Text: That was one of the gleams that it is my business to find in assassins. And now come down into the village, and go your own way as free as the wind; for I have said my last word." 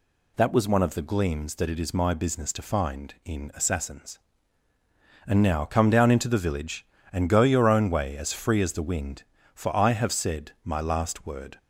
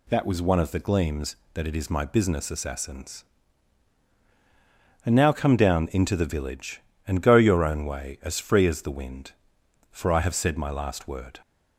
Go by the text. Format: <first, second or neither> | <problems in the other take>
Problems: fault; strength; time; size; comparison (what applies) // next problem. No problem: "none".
first | skips "to find in"; at 2.4 s